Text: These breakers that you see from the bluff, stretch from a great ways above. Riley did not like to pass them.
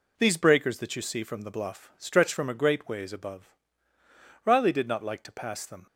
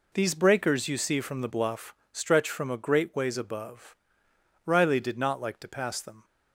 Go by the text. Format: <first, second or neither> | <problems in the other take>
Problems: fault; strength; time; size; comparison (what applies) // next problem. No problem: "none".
first | skips "that"; at 0.8 s